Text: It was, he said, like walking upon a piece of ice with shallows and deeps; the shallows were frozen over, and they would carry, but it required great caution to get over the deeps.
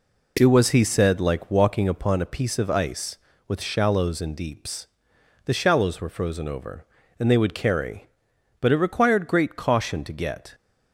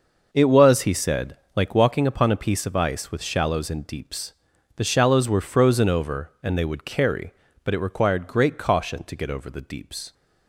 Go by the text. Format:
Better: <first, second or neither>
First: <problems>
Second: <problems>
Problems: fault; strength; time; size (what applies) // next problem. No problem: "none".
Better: second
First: stops before "over the deeps"; at 10.5 s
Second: none